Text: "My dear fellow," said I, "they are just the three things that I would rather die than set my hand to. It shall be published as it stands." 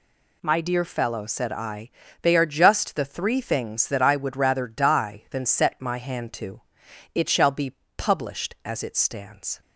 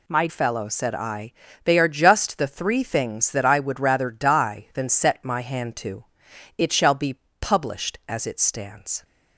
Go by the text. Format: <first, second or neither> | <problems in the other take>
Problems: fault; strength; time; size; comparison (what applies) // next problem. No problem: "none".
first | skips "dear"; at 0.2 s // pauses between "be" and "published"; slight; at 7.1 s; 0.22 s long; slight in the first